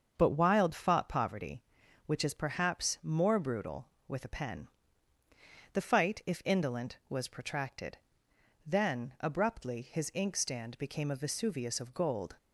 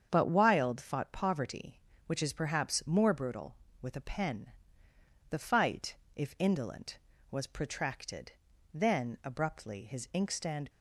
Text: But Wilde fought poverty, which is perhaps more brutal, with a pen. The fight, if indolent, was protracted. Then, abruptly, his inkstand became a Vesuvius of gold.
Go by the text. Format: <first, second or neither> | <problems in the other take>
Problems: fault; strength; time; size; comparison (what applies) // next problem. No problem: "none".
first | starts louder than the rest; strong; until 1.1 s; 7.5 dB; also in the first // stops before "became a Vesuvius of gold"; at 10.7 s